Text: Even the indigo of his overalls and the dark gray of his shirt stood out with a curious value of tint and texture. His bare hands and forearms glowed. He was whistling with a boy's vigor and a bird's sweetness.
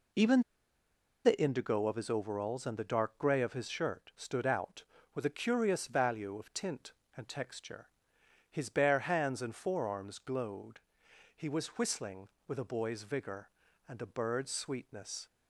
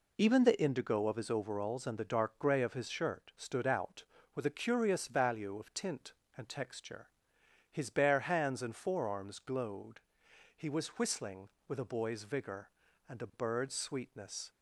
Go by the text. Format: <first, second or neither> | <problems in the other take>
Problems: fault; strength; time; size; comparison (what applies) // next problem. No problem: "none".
second | pauses between "Even" and "the"; noticeable; at 0.4 s; 0.82 s long